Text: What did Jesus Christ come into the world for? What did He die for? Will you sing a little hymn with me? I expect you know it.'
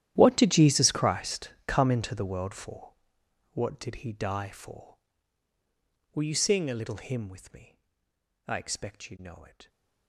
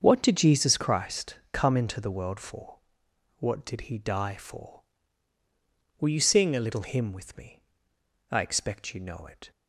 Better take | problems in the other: second | gets quieter; strong; throughout; 20 dB // starts louder than the rest; strong; until 1.1 s; 12 dB; also in the second // pauses between "Christ" and "come"; slight; at 1.5 s; 0.16 s long; slight in the second

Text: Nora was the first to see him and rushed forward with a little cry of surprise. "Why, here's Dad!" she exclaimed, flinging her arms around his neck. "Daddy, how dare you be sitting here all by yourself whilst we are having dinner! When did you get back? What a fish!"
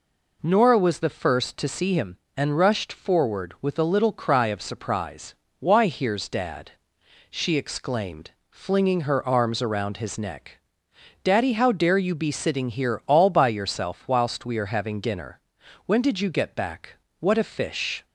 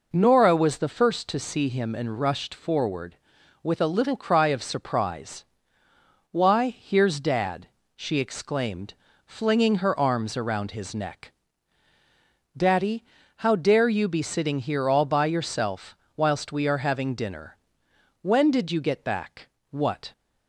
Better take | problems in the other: first | pauses between "yourself" and "whilst"; slight; at 15.9 s; 0.20 s long // stops before "a fish"; at 20.1 s

